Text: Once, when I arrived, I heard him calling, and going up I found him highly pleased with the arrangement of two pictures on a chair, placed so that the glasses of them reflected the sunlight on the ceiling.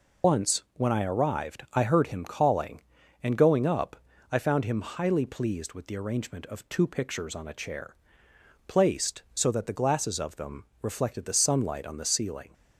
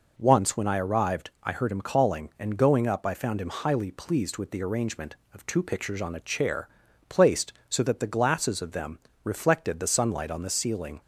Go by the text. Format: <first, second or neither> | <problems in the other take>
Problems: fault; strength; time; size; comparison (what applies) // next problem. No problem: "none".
second | loses the start of "Once"; at 0.2 s; 95 ms // pauses between "up" and "I"; slight; at 3.9 s; 0.34 s long // pauses between "them" and "reflected"; slight; at 10.6 s; 0.18 s long; slight in the second